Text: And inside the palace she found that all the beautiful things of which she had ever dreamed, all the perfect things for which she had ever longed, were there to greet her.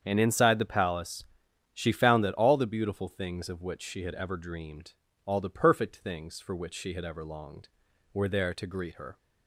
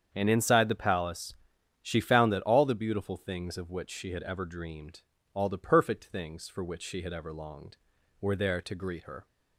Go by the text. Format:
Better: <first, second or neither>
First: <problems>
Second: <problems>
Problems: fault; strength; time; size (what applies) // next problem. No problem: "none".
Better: neither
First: starts louder than the rest; strong; until 1.0 s; 7.5 dB // pauses between "palace" and "she"; noticeable; at 1.2 s; 0.50 s long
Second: starts louder than the rest; strong; until 1.1 s; 7.5 dB // pauses between "palace" and "she"; noticeable; at 1.3 s; 0.48 s long